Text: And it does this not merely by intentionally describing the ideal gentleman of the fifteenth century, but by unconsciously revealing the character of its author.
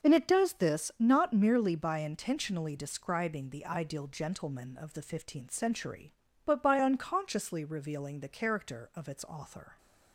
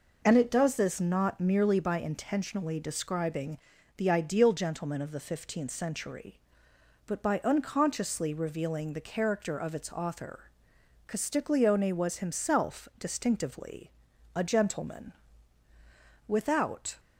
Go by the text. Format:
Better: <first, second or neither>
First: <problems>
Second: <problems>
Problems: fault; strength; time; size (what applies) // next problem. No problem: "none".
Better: first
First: none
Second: pauses between "describing" and "the"; at 3.5 s; 0.40 s long // goes on to say "Castiglione was himself distinctively a gentleman Without"; strong; from 11.0 s on; 5.9 s long